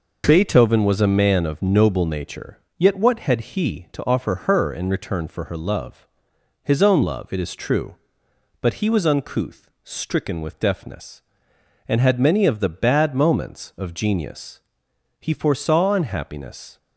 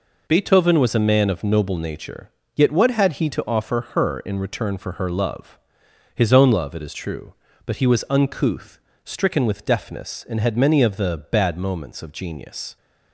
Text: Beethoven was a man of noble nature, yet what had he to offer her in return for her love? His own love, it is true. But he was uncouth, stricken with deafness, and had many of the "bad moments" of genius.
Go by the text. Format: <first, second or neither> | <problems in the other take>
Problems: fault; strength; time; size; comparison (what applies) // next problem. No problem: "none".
second | goes on to say "He foresaw unhappiness"; from 15.2 s on; 1.5 s long